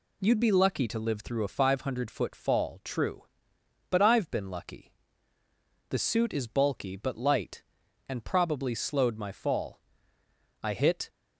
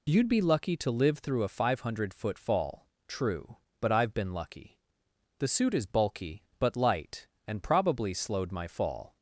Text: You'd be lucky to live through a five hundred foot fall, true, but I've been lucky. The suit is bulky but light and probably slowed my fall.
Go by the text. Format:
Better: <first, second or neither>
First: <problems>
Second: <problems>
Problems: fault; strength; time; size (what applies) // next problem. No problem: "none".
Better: second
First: goes on to say "I hit"; slight; from 10.6 s on; 0.46 s long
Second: none